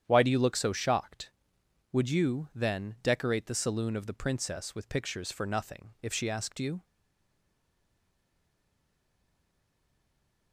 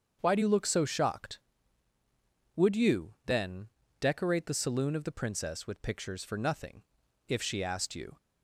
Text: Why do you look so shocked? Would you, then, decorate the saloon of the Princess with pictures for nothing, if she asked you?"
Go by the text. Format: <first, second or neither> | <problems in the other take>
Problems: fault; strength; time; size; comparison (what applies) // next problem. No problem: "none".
second | starts louder than the rest; strong; until 1.0 s; 9.5 dB; also in the second // stays silent after the last word; strong; from 6.8 s on; 3.7 s long